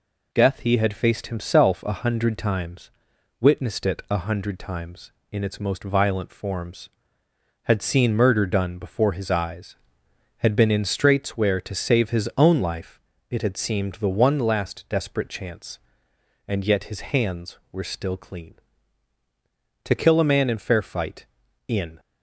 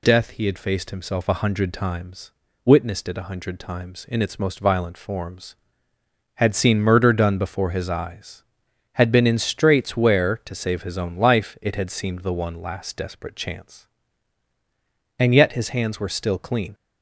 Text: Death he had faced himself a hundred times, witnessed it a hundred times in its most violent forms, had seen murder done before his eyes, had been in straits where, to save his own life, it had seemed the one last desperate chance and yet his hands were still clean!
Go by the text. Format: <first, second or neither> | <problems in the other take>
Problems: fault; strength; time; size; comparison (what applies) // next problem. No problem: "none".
second | goes on to say "To kill a man in fair fight in"; strong; from 19.8 s on; 2.1 s long